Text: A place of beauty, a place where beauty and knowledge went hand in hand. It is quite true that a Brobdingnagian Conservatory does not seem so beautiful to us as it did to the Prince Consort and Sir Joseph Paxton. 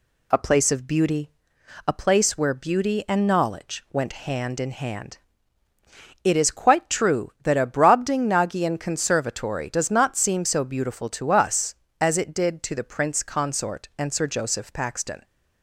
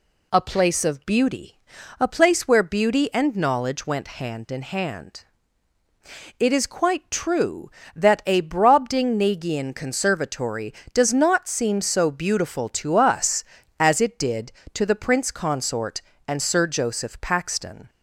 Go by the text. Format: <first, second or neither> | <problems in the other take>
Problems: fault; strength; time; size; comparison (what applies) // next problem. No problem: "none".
neither | none